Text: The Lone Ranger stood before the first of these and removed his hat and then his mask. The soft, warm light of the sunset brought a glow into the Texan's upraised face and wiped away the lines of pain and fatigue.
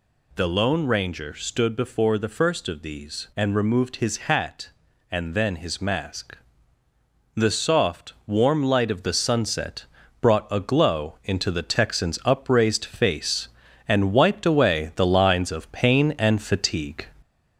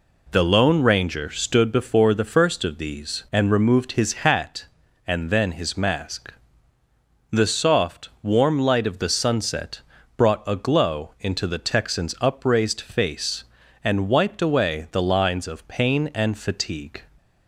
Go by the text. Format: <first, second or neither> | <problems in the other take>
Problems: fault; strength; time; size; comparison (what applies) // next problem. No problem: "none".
second | gets louder; slight; throughout; 2.5 dB // pauses between "sunset" and "brought"; at 9.8 s; 0.38 s long; also in the second